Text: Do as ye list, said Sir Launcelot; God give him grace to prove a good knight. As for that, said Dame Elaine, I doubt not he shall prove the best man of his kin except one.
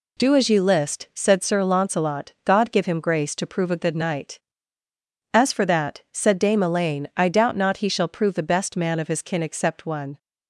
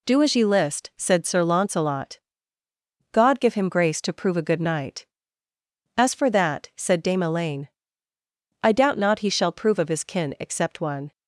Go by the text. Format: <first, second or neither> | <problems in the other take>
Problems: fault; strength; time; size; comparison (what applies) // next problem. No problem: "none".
first | skips "the best man"; at 9.7 s